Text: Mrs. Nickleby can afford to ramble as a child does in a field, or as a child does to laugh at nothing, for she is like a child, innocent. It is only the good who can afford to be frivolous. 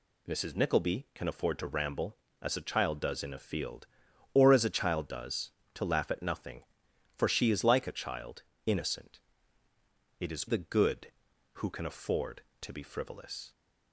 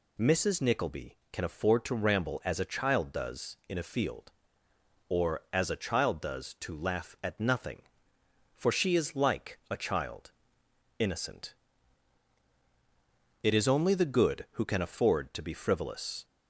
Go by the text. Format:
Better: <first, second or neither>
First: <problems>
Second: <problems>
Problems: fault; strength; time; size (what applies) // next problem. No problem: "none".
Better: second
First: skips "only"; at 10.4 s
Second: none